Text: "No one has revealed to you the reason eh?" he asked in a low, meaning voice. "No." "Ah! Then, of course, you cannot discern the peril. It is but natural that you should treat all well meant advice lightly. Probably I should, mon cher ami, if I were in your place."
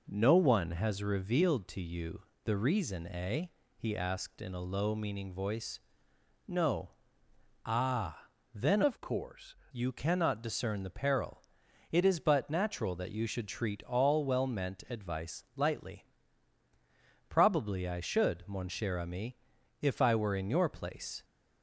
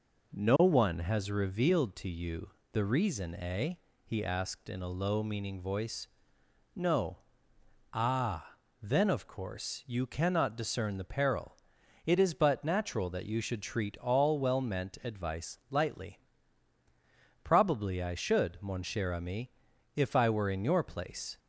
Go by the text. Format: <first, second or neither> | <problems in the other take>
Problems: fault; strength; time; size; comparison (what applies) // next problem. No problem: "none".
second | pauses between "you" and "the"; slight; at 2.2 s; 0.20 s long; slight in the second // changes voice from "of" to "course"; from 8.8 to 9.5 s; 0.7 s long